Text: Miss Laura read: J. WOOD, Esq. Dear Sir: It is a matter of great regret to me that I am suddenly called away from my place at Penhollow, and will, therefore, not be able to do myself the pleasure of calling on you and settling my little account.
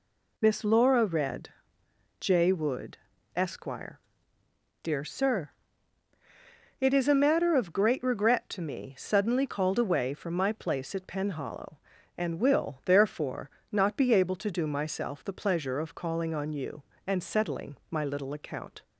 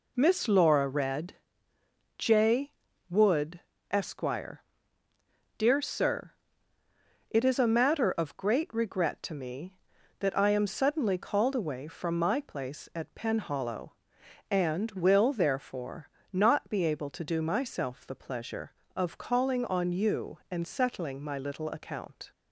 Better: second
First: skips "that I am"; at 8.9 s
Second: none

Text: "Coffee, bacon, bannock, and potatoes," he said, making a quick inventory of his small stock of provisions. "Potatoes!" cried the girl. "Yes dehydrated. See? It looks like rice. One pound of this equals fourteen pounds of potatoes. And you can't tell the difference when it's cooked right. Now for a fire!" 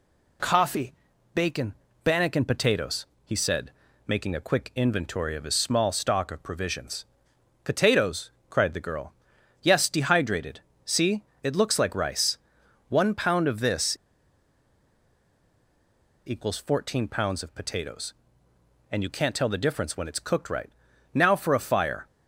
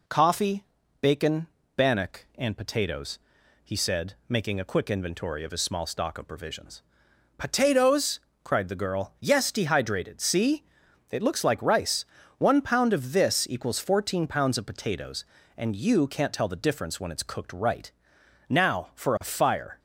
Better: second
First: pauses between "this" and "equals"; strong; at 13.9 s; 2.3 s long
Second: none

